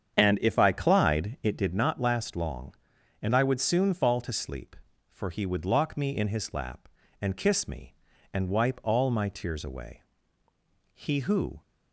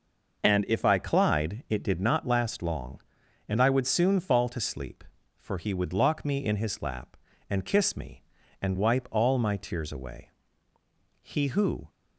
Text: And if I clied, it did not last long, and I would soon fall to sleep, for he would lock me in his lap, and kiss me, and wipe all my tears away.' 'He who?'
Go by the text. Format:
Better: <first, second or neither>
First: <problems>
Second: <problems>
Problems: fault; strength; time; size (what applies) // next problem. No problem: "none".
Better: second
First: starts louder than the rest; strong; until 1.7 s; 8 dB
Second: none